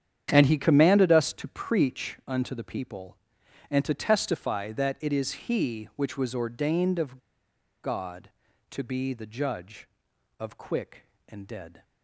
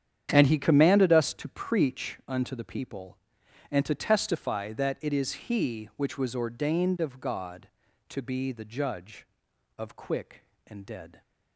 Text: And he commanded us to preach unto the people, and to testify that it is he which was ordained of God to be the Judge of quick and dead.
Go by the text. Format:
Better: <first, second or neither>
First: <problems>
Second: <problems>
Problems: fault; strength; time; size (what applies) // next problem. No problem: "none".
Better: second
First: starts louder than the rest; strong; until 1.3 s; 9 dB // pauses between "of" and "God"; noticeable; at 7.1 s; 0.66 s long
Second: starts louder than the rest; strong; until 1.3 s; 9 dB